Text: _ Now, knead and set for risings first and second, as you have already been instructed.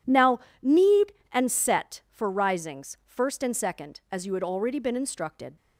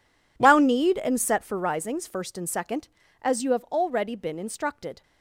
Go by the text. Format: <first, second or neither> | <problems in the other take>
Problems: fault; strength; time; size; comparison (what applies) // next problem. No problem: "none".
second | says "had" for "have"; at 4.3 s